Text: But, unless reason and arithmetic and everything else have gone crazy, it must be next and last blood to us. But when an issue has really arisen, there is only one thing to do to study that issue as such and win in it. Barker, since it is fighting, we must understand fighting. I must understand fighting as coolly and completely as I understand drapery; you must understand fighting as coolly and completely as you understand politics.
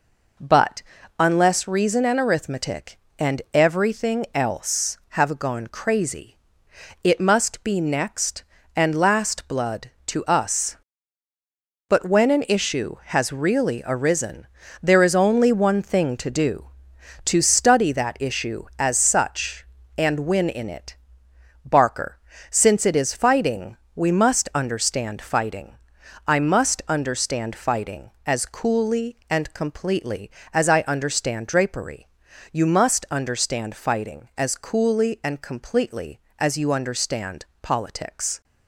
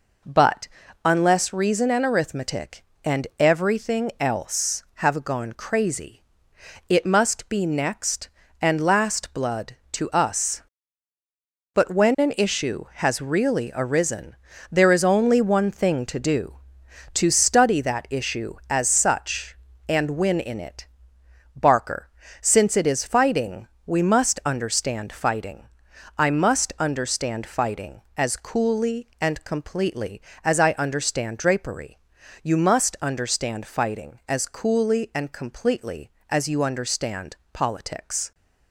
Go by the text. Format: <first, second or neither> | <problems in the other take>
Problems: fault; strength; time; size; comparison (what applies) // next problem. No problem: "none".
neither | pauses between "understand" and "politics"; slight; the same in both